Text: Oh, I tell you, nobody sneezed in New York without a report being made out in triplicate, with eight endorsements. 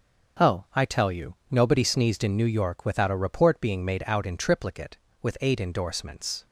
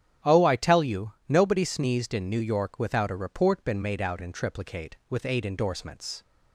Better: first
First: starts louder than the rest; until 1.6 s; 6.5 dB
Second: starts louder than the rest; strong; until 1.3 s; 9.5 dB // says "been" for "being"; at 3.6 s

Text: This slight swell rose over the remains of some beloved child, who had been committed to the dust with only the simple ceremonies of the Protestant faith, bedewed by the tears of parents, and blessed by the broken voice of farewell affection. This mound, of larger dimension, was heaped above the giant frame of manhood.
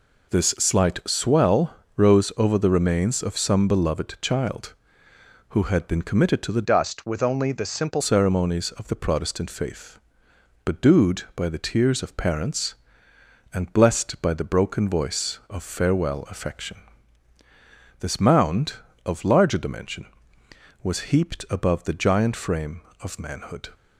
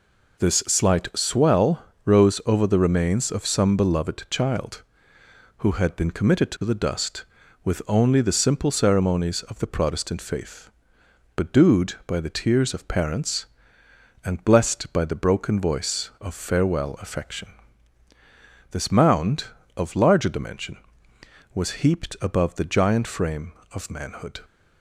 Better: second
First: pauses between "swell" and "rose"; slight; at 1.7 s; 0.22 s long // changes voice from "dust" to "simple"; from 6.6 to 8.0 s; 1.4 s long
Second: pauses between "swell" and "rose"; slight; at 1.8 s; 0.22 s long

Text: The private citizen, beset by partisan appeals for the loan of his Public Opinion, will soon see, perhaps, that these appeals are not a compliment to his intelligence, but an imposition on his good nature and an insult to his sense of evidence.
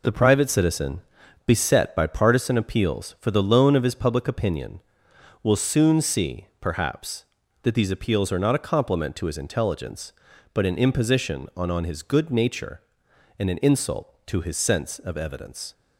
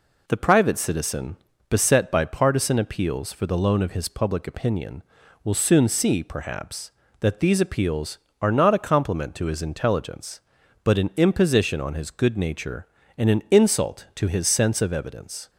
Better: second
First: says "on" twice; at 11.7 s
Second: none

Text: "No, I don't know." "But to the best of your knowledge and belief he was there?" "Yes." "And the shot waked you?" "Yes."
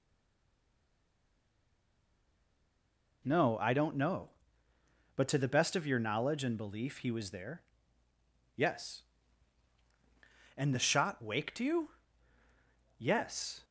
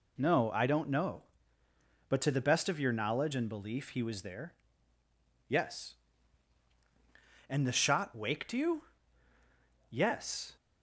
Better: second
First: stays silent before the first word; strong; until 3.2 s; 3.2 s long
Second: none

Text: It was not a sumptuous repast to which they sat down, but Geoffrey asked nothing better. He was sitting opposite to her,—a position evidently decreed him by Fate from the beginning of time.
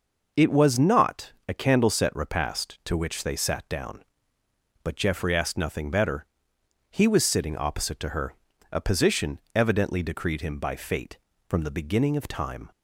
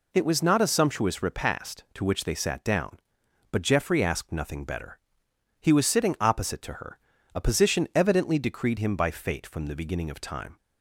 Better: second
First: pauses between "not" and "a"; slight; at 1.3 s; 0.16 s long // says "candleset" for "sumptuous"; at 1.5 s // pauses between "position" and "evidently"; slight; at 9.3 s; 0.16 s long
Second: none

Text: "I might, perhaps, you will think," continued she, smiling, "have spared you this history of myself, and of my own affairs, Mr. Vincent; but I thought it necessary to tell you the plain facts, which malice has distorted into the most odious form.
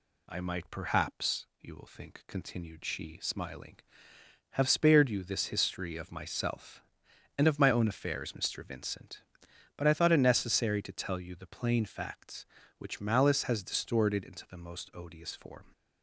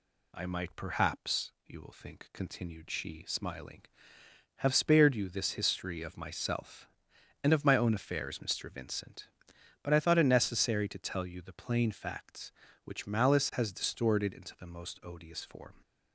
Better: neither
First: none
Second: none

